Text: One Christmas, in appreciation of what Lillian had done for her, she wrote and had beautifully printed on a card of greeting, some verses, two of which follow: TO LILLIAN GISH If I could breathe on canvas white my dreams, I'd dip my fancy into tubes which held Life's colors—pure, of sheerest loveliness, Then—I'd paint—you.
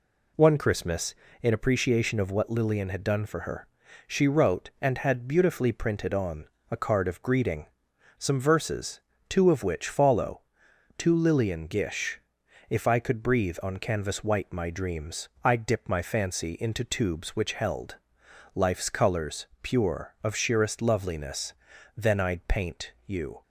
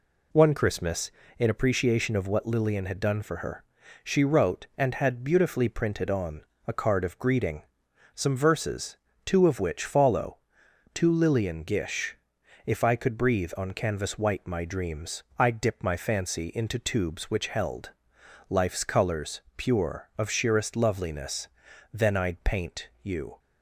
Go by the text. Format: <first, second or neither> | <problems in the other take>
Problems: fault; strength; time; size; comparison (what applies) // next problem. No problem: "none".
neither | pauses between "on" and "a"; slight; the same in both // pauses between "GISH" and "If"; noticeable; the same in both // pauses between "held" and "Life's"; noticeable; the same in both